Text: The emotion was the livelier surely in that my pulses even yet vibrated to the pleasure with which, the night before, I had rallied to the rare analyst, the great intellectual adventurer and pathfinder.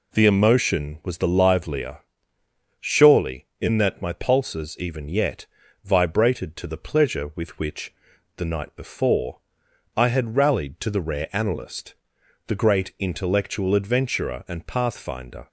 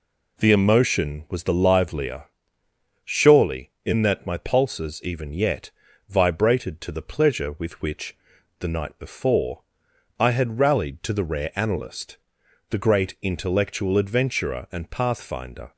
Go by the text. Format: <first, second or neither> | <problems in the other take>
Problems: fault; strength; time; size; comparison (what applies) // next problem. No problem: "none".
neither | pauses between "livelier" and "surely"; noticeable; the same in both // pauses between "yet" and "vibrated"; the same in both